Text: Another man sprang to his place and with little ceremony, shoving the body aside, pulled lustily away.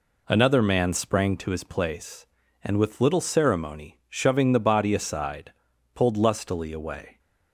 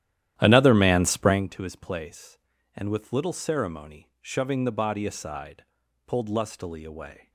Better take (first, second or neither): first